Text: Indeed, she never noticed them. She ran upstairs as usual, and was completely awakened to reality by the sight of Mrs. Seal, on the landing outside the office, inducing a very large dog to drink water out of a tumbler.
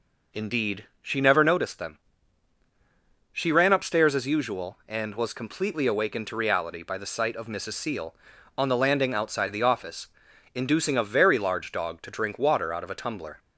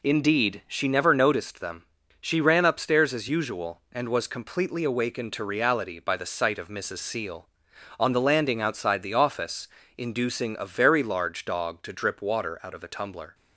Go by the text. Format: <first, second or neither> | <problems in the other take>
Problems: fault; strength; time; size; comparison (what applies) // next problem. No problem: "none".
first | says "drip" for "drink"; at 11.9 s